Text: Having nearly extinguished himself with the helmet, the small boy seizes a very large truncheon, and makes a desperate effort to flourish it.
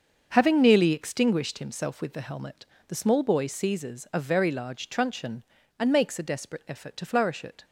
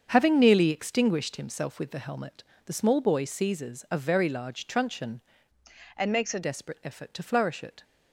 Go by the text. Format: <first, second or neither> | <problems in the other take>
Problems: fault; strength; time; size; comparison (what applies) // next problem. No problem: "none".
first | starts louder than the rest; strong; until 1.1 s; 7 dB; also in the first // changes voice from "and" to "a"; from 5.9 to 6.4 s; 0.5 s long